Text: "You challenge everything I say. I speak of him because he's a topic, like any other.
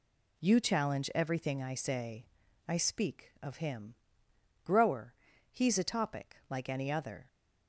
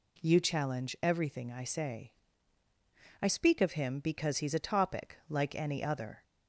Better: second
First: says "grower" for "because"; at 4.6 s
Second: none

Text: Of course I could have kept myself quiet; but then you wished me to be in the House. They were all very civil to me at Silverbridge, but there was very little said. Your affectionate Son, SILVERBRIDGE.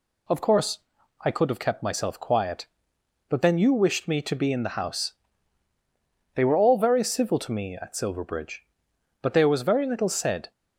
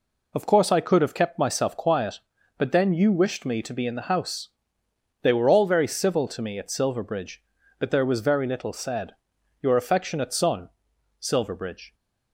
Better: second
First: pauses between "course" and "I"; noticeable; at 0.7 s; 0.46 s long // stops before "Your affectionate Son SILVERBRIDGE"; at 10.5 s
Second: none

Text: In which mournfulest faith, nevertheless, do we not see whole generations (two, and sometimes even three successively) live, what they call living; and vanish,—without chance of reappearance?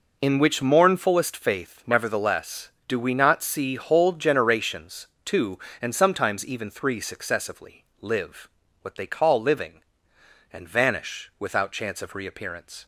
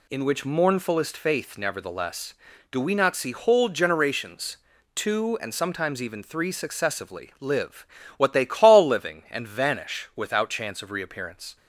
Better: neither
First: none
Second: none

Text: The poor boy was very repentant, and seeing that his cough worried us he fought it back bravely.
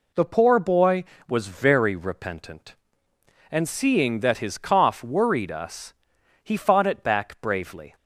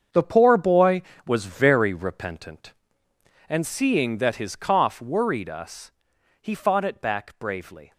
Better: first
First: pauses between "us" and "he"; noticeable; at 5.9 s; 0.52 s long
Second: gets quieter; strong; throughout; 11.5 dB // pauses between "us" and "he"; noticeable; at 5.9 s; 0.52 s long

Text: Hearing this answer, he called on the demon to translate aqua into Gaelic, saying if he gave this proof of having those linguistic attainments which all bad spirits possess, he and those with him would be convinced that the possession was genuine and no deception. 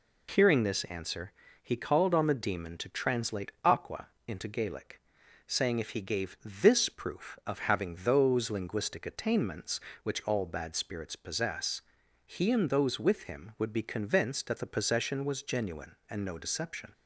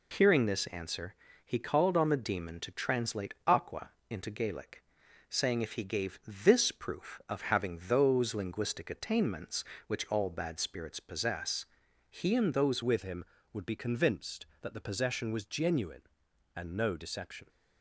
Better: first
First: pauses between "aqua" and "into"; slight; at 4.0 s; 0.18 s long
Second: pauses between "aqua" and "into"; slight; at 3.9 s; 0.18 s long // changes voice at "with"; from 12.8 s on; 4.6 s long

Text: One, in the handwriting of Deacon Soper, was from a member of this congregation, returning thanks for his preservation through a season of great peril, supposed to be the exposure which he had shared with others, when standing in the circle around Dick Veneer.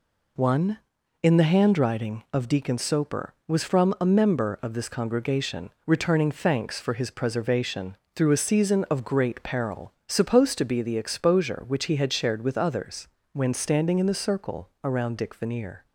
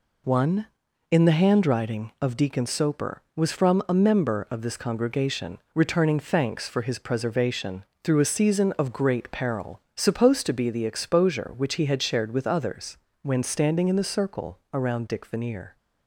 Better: neither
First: pauses between "preservation" and "through"; slight; at 7.9 s; 0.18 s long // pauses between "circle" and "around"; slight; at 14.6 s; 0.16 s long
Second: pauses between "preservation" and "through"; slight; at 7.8 s; 0.18 s long // pauses between "circle" and "around"; slight; at 14.5 s; 0.16 s long

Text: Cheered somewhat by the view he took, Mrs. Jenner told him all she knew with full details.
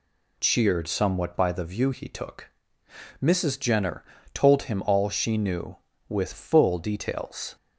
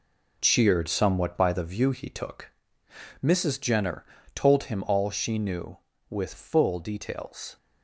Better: first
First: pauses between "Jenner" and "told"; slight; at 4.0 s; 0.30 s long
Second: gets quieter; strong; throughout; 8.5 dB // pauses between "Jenner" and "told"; slight; at 4.0 s; 0.30 s long

